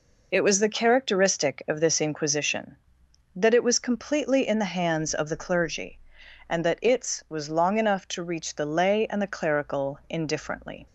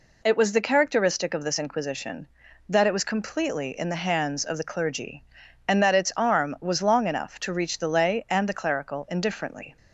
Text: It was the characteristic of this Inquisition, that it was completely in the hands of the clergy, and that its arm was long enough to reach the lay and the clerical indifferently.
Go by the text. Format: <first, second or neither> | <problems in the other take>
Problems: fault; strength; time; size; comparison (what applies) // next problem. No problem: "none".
second | skips "arm"; at 7.2 s